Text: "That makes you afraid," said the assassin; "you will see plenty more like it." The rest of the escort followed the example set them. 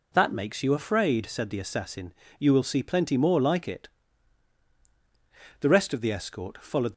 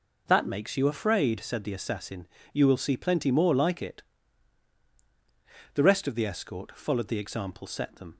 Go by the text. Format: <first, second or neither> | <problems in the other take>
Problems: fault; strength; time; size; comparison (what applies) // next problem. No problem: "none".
second | stops before "the example set them"; at 6.9 s